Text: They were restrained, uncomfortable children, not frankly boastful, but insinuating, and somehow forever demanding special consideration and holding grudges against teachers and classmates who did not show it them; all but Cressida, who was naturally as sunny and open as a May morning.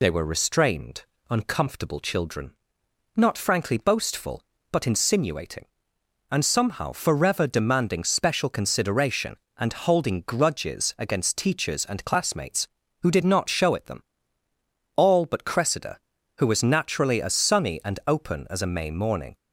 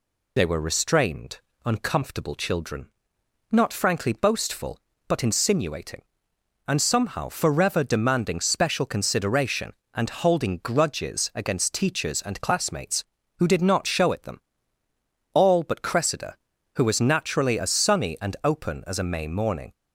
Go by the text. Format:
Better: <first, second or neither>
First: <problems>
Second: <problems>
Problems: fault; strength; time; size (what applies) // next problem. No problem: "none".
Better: neither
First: none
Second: none